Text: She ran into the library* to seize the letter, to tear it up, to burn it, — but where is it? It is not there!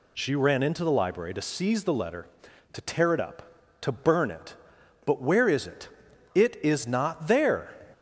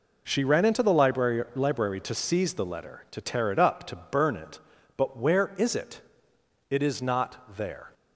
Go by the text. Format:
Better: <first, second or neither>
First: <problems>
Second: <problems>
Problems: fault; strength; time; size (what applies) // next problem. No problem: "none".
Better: first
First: none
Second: says "library" twice; at 1.5 s